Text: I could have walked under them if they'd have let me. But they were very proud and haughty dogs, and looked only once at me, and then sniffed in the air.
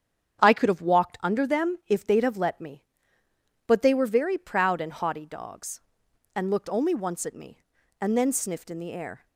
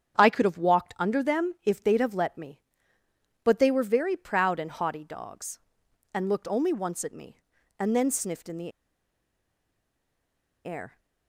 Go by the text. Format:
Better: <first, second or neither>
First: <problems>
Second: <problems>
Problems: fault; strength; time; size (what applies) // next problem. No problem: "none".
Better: first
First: starts louder than the rest; strong; until 1.4 s; 8.5 dB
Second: starts louder than the rest; strong; until 1.2 s; 8.5 dB // pauses between "the" and "air"; strong; at 8.7 s; 1.9 s long